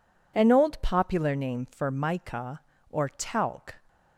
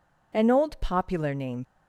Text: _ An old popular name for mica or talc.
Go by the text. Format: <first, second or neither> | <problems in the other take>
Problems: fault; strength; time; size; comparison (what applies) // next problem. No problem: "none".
first | stops before "for mica or talc"; at 1.6 s